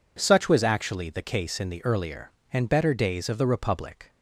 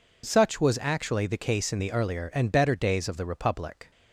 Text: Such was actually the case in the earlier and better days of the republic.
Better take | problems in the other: neither | none

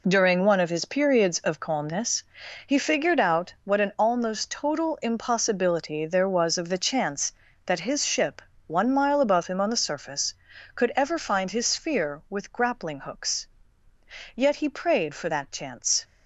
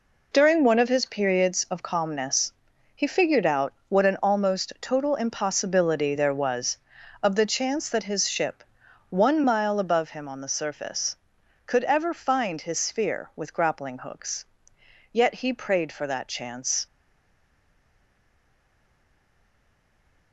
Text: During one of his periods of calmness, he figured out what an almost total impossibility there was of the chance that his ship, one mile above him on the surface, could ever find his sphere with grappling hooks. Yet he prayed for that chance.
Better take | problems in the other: first | pauses between "out" and "what"; slight; at 3.7 s; 0.16 s long // stays silent after the last word; strong; from 16.8 s on; 3.5 s long

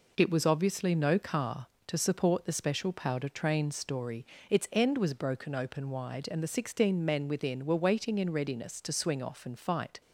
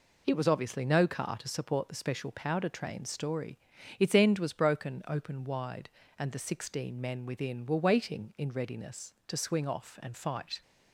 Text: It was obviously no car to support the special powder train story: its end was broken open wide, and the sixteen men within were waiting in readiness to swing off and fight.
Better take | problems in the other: neither | none

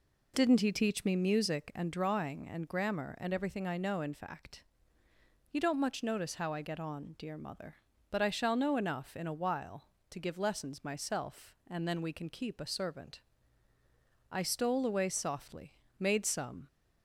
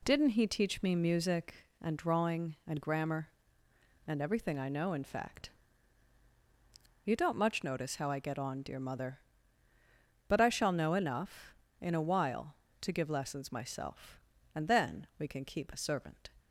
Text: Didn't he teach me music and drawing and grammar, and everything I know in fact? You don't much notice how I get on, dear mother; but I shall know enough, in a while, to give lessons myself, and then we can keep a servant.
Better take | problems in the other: second | goes on to say "I stole away softly made some"; strong; from 14.2 s on; 2.3 s long

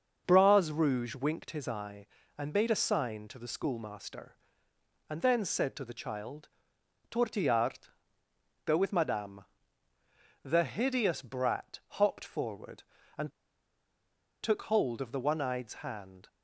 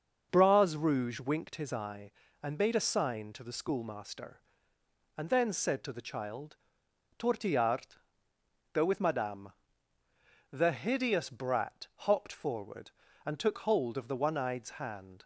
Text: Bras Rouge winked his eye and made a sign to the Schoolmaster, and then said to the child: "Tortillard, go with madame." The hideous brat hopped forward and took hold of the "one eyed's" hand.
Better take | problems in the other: second | starts louder than the rest; until 1.2 s; 6 dB; also in the second // pauses between "and" and "took"; at 13.2 s; 1.1 s long

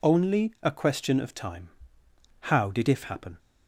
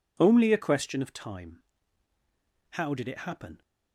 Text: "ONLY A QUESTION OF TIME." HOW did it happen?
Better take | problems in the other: second | says "if" for "it"; at 2.8 s

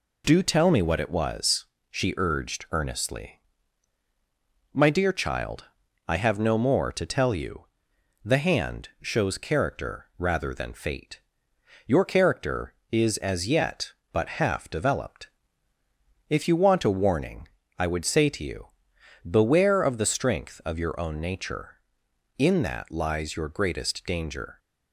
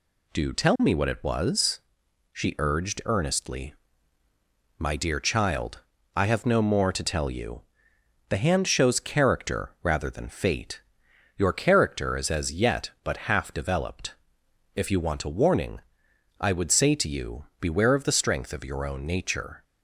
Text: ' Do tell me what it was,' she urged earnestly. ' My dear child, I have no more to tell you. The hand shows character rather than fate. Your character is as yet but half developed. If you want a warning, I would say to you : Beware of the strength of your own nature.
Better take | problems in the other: second | goes on to say "In that lies your greatest danger"; strong; from 22.3 s on; 2.2 s long

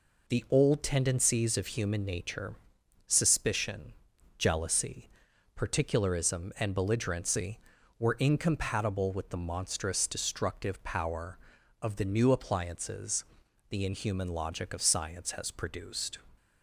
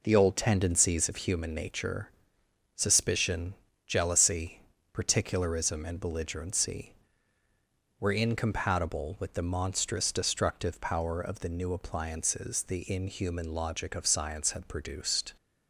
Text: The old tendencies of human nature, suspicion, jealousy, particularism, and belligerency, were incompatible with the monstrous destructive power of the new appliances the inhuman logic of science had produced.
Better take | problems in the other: second | pauses between "appliances" and "the"; at 13.2 s; 0.44 s long // says "has" for "had"; at 15.3 s

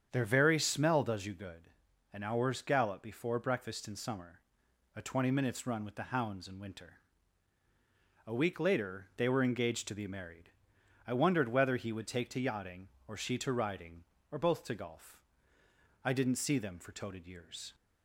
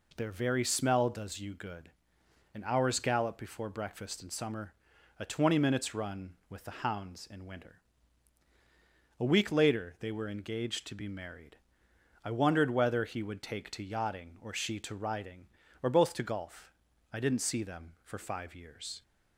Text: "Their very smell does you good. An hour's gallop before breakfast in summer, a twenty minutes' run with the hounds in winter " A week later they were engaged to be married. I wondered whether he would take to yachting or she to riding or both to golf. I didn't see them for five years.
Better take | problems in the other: second | starts louder than the rest; strong; until 1.1 s; 8 dB // says "toted" for "five"; at 16.9 s

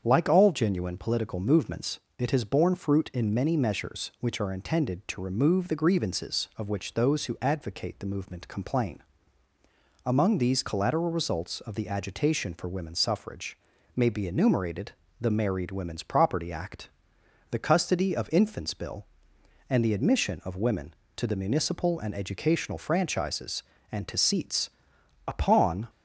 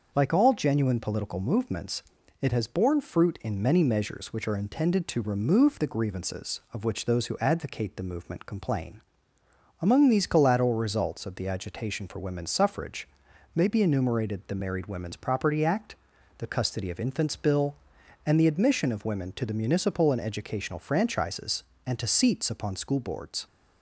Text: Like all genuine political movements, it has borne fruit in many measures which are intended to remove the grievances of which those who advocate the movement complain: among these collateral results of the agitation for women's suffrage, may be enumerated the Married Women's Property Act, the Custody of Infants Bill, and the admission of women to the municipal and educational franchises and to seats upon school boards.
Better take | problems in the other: second | starts louder than the rest; strong; until 1.0 s; 7.5 dB; also in the second // pauses between "enumerated" and "the"; slight; at 14.9 s; 0.26 s long // pauses between "seats" and "upon"; noticeable; at 24.6 s; 0.58 s long // stops before "school boards"; at 25.8 s

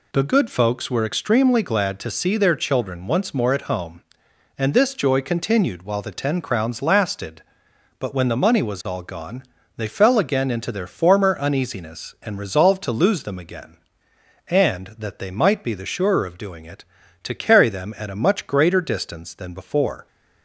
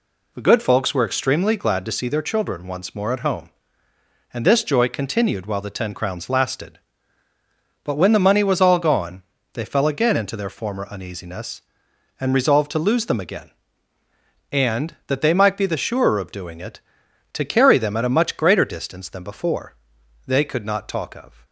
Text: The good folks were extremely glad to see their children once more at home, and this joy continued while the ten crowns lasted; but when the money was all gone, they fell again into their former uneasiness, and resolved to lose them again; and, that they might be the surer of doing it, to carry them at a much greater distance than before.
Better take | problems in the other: first | goes on to say "They could not talk of"; noticeable; from 20.2 s on; 1.2 s long

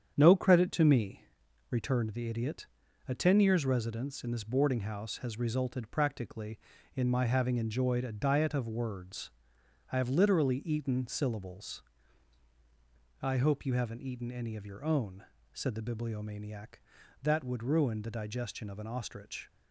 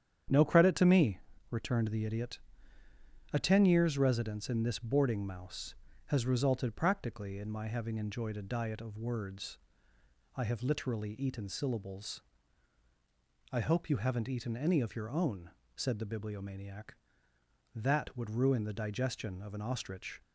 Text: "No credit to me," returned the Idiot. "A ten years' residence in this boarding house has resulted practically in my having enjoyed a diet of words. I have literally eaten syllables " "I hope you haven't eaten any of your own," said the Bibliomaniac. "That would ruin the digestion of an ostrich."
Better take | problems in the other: first | starts louder than the rest; strong; until 1.6 s; 9 dB; strong in the first // says "mouse" for "house"; at 5.2 s

